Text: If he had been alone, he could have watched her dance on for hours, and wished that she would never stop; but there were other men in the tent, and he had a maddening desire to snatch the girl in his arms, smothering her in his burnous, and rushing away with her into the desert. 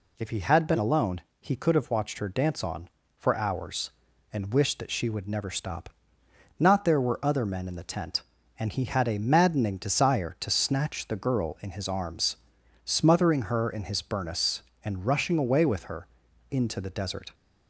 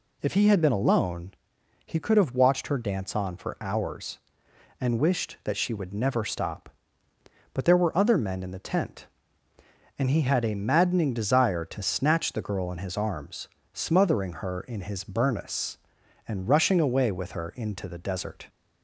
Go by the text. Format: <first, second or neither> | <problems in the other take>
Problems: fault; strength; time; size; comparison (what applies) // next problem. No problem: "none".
second | says "not" for "but"; at 6.5 s // pauses between "her" and "into"; at 16.0 s; 0.42 s long